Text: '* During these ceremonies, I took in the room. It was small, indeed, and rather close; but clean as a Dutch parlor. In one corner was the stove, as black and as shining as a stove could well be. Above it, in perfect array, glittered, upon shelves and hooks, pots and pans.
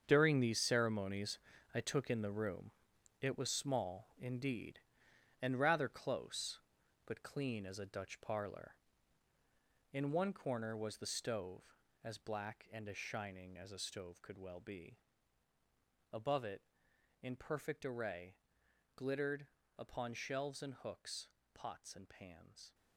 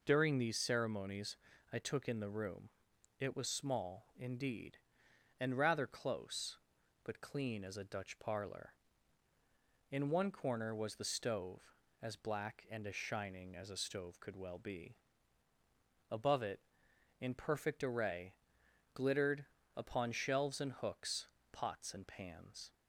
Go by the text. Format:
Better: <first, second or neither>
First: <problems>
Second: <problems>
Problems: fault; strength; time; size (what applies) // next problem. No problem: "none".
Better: second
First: gets quieter; strong; throughout; 11.5 dB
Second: none